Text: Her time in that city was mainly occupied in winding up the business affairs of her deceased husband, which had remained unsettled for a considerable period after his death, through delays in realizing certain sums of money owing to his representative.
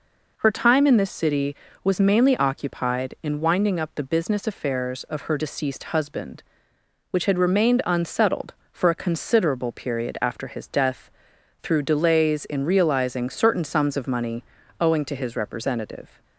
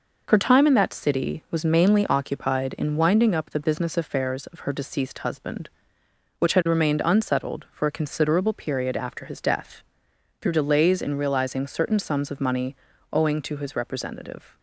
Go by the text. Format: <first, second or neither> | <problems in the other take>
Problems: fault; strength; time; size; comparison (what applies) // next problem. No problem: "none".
second | says "this" for "that"; at 0.9 s // pauses between "money" and "owing"; at 14.4 s; 0.38 s long; slight in the second